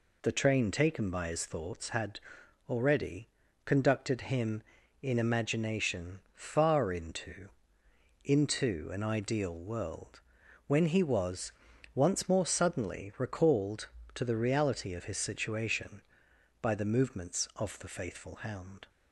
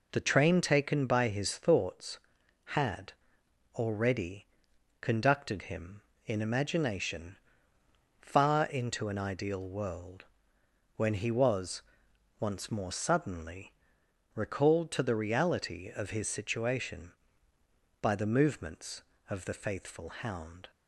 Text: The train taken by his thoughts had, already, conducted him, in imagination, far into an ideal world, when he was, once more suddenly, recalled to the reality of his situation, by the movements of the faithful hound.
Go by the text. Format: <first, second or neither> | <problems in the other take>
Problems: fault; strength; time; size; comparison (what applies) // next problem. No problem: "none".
second | says "into" twice; at 8.2 s